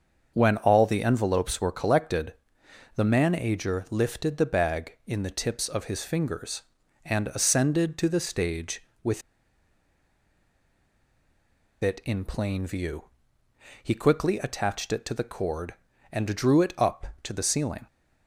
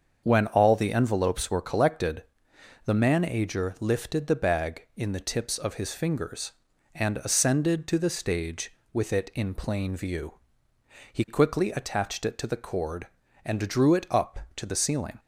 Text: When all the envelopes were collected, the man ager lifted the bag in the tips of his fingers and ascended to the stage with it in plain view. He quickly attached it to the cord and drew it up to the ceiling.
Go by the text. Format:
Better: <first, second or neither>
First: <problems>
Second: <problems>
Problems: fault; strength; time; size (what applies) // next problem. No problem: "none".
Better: second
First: starts louder than the rest; until 1.3 s; 6.5 dB // pauses between "with" and "it"; strong; at 9.2 s; 2.6 s long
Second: starts louder than the rest; until 1.2 s; 6.5 dB